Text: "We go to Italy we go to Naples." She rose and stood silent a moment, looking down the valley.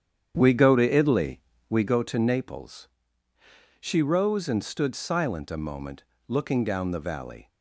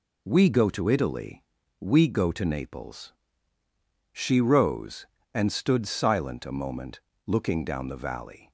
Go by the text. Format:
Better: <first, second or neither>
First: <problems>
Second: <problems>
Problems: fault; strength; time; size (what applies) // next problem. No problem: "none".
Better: second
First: starts louder than the rest; strong; until 2.0 s; 8.5 dB // pauses between "Italy" and "we"; slight; at 1.3 s; 0.30 s long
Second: pauses between "Italy" and "we"; at 1.4 s; 0.38 s long